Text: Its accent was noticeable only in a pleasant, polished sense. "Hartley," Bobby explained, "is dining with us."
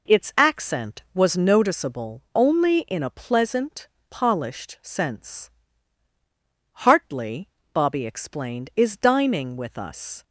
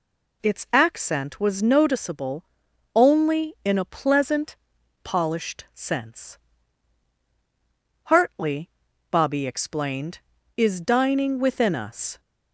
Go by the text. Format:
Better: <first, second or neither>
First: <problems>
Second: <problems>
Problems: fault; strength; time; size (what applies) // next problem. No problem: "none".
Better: first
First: none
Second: pauses between "noticeable" and "only"; noticeable; at 2.4 s; 0.50 s long // says "within" for "with"; at 11.4 s